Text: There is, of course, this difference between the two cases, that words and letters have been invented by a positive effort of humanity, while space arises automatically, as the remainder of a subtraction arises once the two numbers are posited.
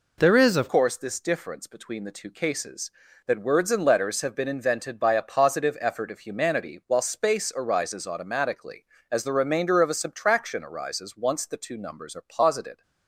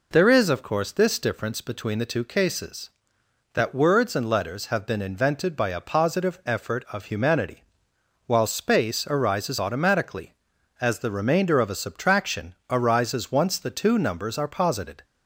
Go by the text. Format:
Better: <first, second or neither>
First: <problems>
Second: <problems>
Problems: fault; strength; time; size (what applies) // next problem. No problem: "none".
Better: second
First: changes voice at "course"; from 0.6 s on; 12.2 s long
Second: none